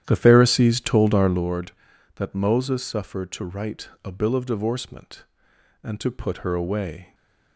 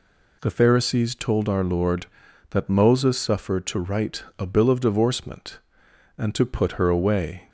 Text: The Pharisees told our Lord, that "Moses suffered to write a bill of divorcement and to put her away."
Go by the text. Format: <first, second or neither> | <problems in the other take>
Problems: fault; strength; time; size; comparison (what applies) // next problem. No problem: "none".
second | starts louder than the rest; strong; until 1.5 s; 11 dB // pauses between "write" and "a"; slight; at 3.8 s; 0.16 s long; slight in the second // stays silent after the last word; slight; from 7.0 s on; 0.5 s long